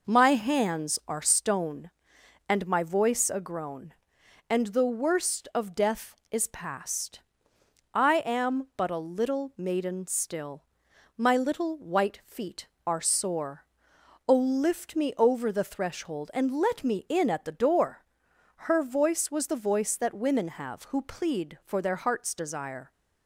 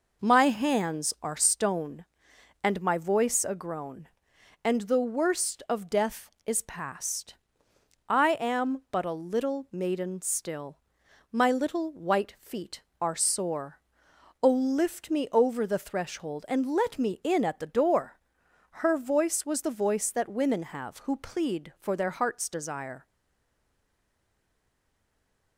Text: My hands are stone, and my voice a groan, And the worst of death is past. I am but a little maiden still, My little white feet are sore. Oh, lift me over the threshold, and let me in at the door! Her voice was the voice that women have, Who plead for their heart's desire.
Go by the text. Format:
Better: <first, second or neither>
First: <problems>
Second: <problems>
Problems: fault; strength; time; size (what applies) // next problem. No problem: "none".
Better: first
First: none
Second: stays silent after the last word; strong; from 23.0 s on; 2.5 s long